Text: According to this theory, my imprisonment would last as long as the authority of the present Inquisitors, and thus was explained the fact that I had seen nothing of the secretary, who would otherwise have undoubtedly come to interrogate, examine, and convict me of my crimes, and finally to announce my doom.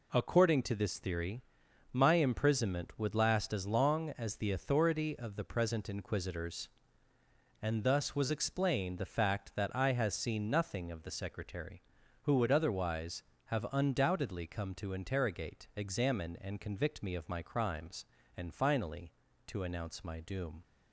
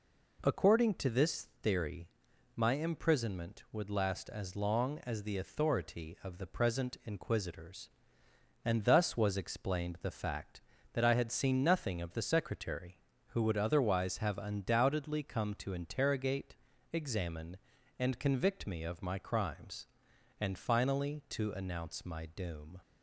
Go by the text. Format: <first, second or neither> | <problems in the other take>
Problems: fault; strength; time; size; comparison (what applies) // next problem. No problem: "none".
second | says "has" for "had"; at 9.9 s